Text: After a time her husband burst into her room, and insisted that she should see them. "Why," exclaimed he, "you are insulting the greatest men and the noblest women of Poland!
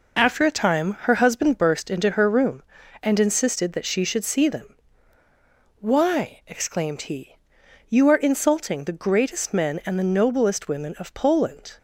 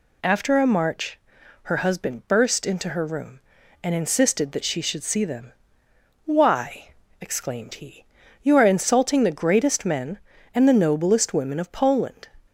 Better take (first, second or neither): first